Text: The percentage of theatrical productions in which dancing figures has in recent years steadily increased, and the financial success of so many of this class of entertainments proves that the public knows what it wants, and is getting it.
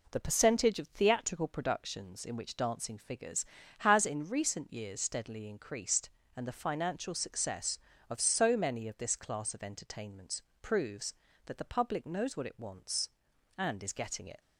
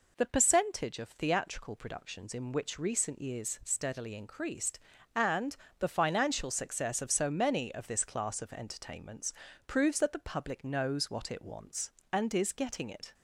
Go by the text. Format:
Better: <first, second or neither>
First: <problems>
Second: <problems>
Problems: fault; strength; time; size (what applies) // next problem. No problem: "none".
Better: first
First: pauses between "entertainments" and "proves"; slight; at 10.4 s; 0.20 s long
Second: skips "dancing figures has in"; at 2.7 s // pauses between "and" and "the"; slight; at 5.5 s; 0.24 s long // pauses between "entertainments" and "proves"; slight; at 9.3 s; 0.34 s long